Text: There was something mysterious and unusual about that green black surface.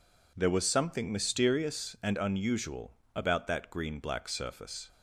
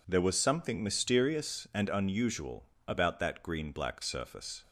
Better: neither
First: pauses between "unusual" and "about"; slight; at 2.9 s; 0.22 s long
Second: pauses between "unusual" and "about"; slight; at 2.6 s; 0.22 s long

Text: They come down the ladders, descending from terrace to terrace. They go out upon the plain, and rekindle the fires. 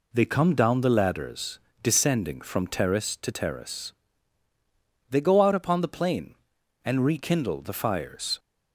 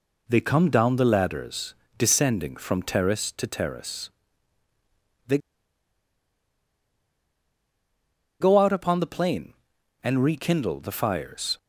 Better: first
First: none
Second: pauses between "They" and "go"; strong; at 5.3 s; 3.0 s long

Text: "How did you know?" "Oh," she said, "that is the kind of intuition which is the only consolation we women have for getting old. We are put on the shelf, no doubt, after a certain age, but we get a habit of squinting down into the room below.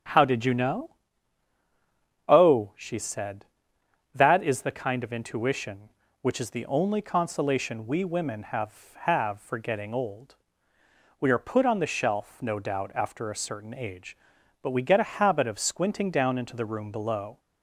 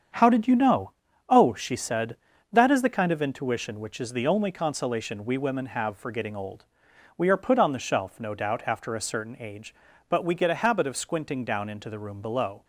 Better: second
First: starts louder than the rest; strong; until 2.4 s; 9 dB // says "have" twice; at 9.0 s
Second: starts louder than the rest; strong; until 1.5 s; 8 dB

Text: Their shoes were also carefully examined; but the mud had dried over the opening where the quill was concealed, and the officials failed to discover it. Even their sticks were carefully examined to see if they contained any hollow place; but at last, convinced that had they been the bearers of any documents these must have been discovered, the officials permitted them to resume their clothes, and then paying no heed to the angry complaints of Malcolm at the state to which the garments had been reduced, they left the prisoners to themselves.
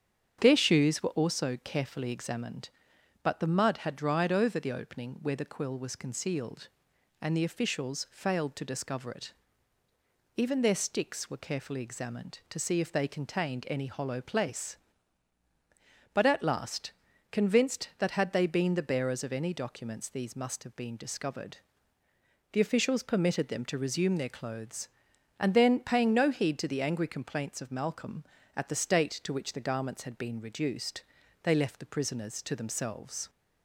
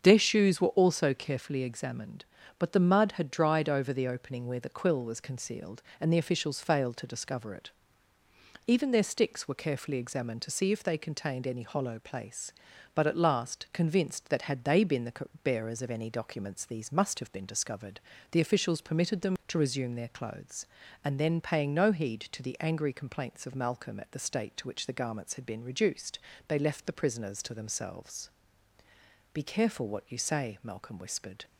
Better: first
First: starts louder than the rest; strong; until 1.4 s; 8 dB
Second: starts louder than the rest; until 1.0 s; 7 dB // pauses between "the" and "bearers"; slight; at 15.1 s; 0.32 s long // goes on to say "Be careful what you say Malcolm whispered"; strong; from 29.3 s on; 2.1 s long

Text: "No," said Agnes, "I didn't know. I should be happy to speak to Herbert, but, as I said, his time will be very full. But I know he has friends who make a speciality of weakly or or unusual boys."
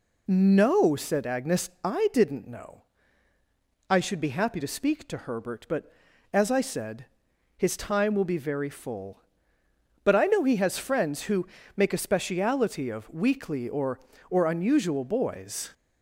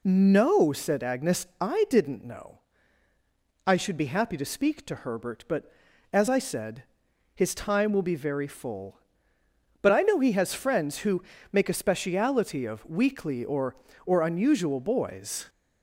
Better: neither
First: pauses between "who" and "make"; slight; at 11.4 s; 0.28 s long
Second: pauses between "who" and "make"; slight; at 11.2 s; 0.28 s long

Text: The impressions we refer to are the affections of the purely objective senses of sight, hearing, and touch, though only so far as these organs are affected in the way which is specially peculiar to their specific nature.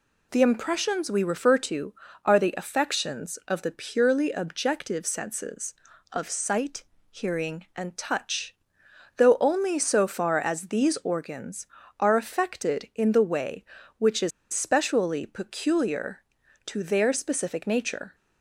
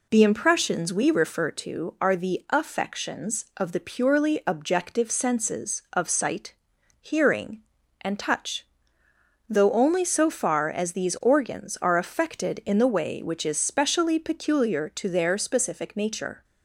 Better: second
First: pauses between "is" and "specially"; slight; at 14.3 s; 0.22 s long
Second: none

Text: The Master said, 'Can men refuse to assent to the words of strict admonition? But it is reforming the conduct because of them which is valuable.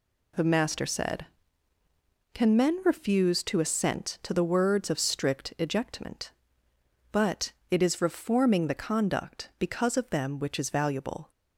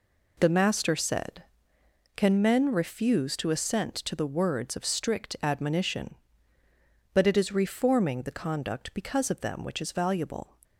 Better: second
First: says "ejectment" for "admonition"; at 5.5 s // pauses between "But" and "it"; slight; at 7.5 s; 0.18 s long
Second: none

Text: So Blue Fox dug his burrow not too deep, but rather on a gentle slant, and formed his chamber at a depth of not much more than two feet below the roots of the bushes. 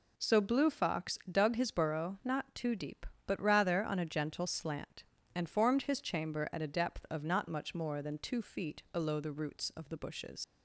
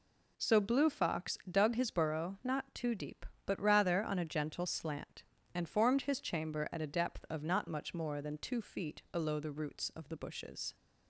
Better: second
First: leaves "bushes" unfinished; at 10.4 s; 110 ms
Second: none

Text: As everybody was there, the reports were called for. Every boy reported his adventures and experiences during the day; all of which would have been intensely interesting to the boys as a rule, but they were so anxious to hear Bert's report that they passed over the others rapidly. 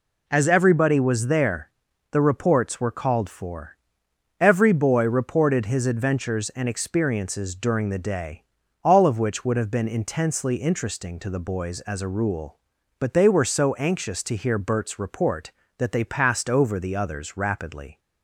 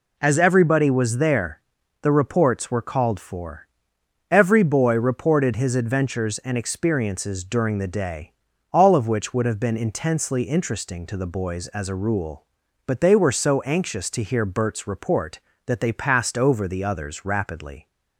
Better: neither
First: none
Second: none

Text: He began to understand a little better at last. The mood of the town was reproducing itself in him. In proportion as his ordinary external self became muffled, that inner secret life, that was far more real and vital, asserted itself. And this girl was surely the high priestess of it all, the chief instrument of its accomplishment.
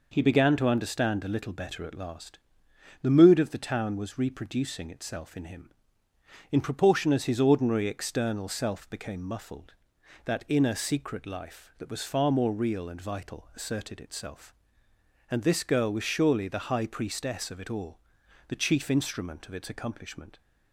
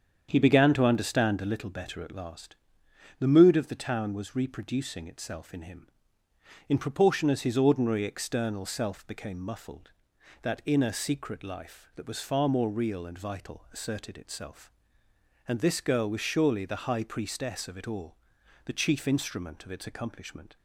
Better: first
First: none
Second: starts louder than the rest; strong; until 1.7 s; 7.5 dB

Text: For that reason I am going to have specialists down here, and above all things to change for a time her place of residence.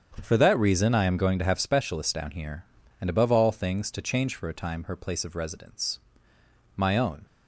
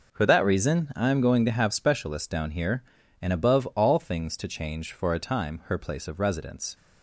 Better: second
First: starts louder than the rest; strong; until 1.2 s; 8 dB // goes on to say "My own"; from 6.7 s on; 0.50 s long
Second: none

